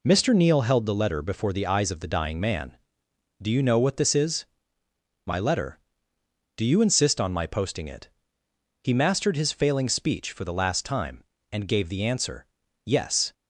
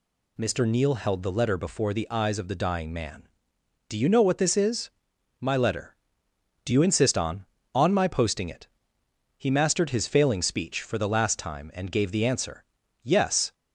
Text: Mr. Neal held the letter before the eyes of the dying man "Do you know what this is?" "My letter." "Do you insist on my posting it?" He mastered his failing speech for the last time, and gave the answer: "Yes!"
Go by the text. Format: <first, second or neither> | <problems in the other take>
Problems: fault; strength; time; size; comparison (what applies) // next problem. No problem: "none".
first | says "on" twice; at 7.7 s